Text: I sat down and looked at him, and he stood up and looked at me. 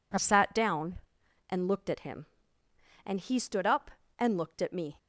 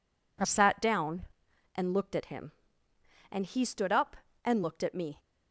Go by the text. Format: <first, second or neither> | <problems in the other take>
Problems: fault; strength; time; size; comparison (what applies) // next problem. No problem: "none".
neither | none